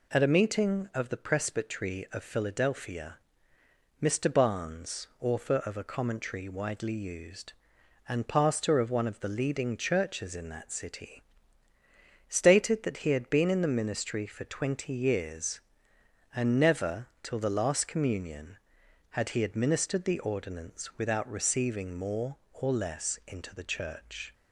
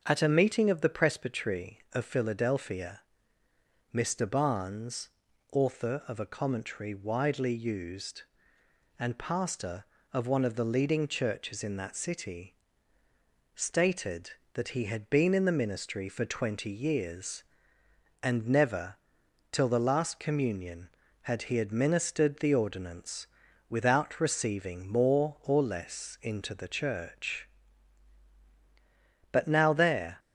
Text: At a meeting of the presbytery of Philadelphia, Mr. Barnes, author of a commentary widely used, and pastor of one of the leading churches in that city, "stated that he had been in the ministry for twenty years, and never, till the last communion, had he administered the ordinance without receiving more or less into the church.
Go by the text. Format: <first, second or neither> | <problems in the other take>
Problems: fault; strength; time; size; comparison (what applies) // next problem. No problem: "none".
first | starts louder than the rest; until 1.0 s; 6.5 dB // pauses between "ordinance" and "without"; at 23.2 s; 0.42 s long // goes on to say "But now there"; noticeable; from 29.3 s on; 0.84 s long